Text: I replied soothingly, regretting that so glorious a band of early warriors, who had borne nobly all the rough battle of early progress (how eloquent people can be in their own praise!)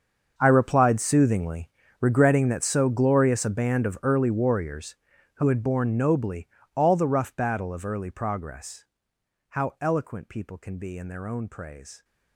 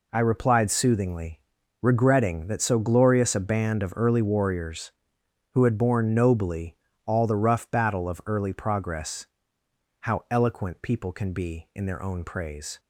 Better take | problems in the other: second | gets quieter; strong; throughout; 18.5 dB // pauses between "nobly" and "all"; slight; at 6.4 s; 0.28 s long; slight in the second

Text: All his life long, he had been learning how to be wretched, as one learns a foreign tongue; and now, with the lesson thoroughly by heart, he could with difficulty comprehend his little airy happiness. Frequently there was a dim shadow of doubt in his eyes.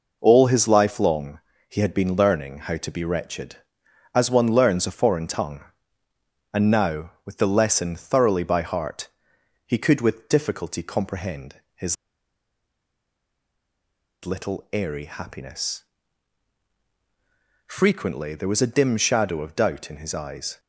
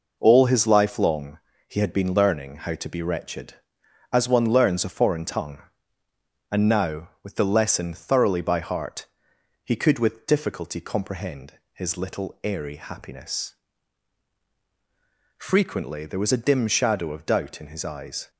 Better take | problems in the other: second | pauses between "comprehend" and "his"; slight; at 11.5 s; 0.18 s long; slight in the second // pauses between "his" and "little"; strong; at 11.9 s; 2.2 s long

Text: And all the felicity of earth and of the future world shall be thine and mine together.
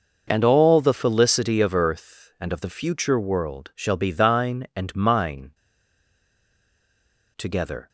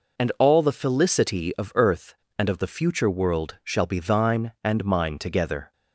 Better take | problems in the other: second | pauses between "mine" and "together"; strong; at 5.5 s; 1.8 s long

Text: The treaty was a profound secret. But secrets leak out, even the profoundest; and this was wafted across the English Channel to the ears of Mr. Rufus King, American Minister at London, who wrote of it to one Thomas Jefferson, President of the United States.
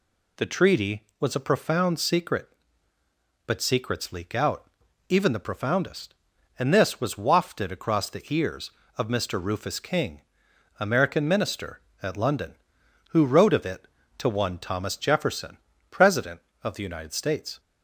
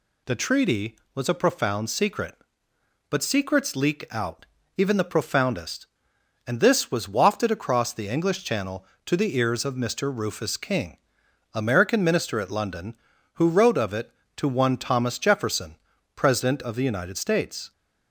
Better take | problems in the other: second | skips "the English Channel to"; at 8.0 s

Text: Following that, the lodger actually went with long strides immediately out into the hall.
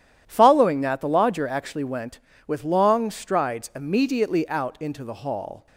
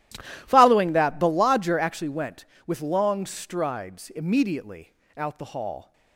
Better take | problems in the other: first | starts louder than the rest; strong; until 1.4 s; 14.5 dB; strong in the first // pauses between "immediately" and "out"; slight; at 4.9 s; 0.24 s long // skips "into"; at 5.3 s

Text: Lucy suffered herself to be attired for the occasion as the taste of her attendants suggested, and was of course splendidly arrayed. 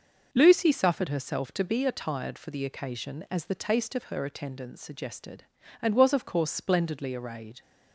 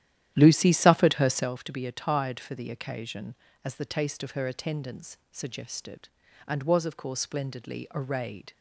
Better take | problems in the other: first | starts louder than the rest; strong; until 1.6 s; 12 dB

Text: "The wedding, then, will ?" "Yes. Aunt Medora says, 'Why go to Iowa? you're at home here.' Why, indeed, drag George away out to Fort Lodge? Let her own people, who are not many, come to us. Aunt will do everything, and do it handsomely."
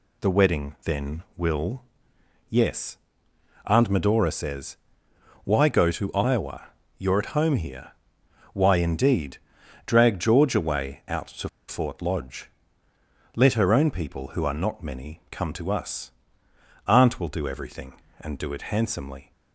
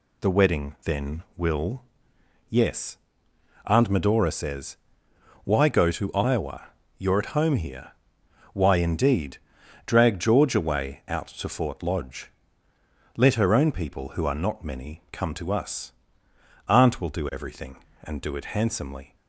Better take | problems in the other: second | pauses between "to" and "Fort"; slight; at 11.4 s; 0.21 s long

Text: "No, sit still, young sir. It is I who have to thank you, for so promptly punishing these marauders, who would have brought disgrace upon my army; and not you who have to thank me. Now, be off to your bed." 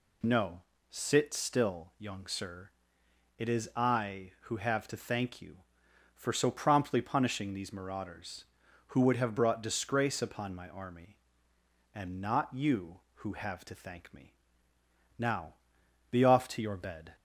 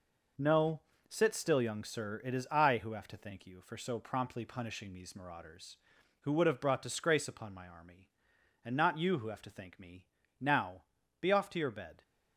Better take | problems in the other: first | gets quieter; throughout; 7 dB

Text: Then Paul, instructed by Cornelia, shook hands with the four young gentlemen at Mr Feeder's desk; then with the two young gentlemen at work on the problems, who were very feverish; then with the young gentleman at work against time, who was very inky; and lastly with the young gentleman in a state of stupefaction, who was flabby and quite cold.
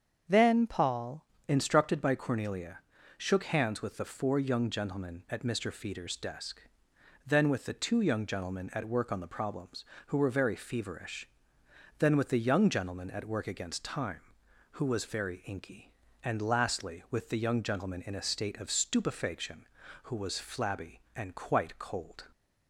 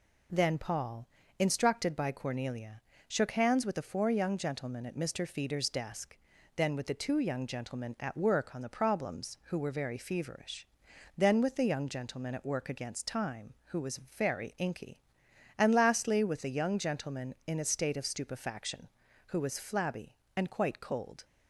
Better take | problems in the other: second | starts louder than the rest; strong; until 1.5 s; 7 dB // changes voice at "instructed"; from 1.4 s on; 20.8 s long

